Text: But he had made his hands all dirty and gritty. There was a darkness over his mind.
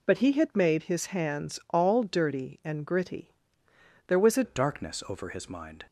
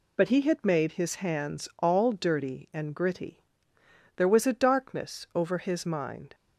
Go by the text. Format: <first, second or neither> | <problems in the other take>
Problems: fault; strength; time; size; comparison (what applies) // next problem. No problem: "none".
second | changes voice at "darkness"; from 4.4 s on; 1.4 s long